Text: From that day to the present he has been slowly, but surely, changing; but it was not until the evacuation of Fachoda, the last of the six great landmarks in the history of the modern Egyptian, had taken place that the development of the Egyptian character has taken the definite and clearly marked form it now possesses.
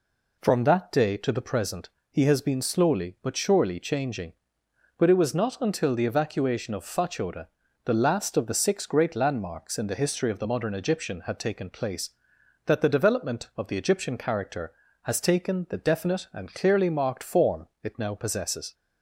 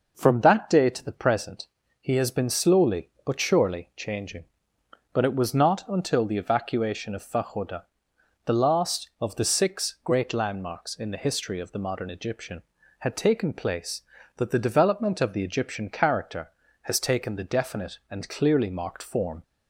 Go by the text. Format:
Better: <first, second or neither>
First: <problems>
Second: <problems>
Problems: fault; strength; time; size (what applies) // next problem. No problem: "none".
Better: first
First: pauses between "present" and "he"; slight; at 1.8 s; 0.22 s long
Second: pauses between "present" and "he"; slight; at 1.6 s; 0.34 s long // stops before "it now possesses"; at 19.4 s